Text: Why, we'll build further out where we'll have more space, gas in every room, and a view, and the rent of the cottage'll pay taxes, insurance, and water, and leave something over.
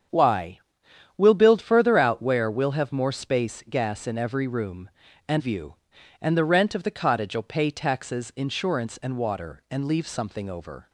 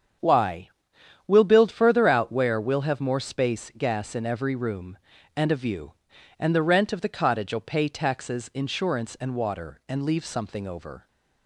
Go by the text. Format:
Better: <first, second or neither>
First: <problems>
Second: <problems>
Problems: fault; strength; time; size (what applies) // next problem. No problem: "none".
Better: second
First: starts louder than the rest; strong; until 1.7 s; 7.5 dB // skips "a"; at 5.4 s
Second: starts louder than the rest; strong; until 1.8 s; 7.5 dB